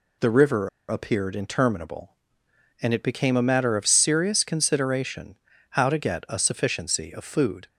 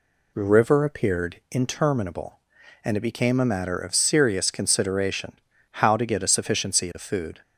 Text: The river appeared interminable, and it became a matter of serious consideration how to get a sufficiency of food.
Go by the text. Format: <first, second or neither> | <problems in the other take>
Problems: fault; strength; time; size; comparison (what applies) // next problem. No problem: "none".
second | pauses between "river" and "appeared"; slight; at 0.6 s; 0.20 s long // pauses between "consideration" and "how"; slight; at 5.3 s; 0.32 s long; also in the second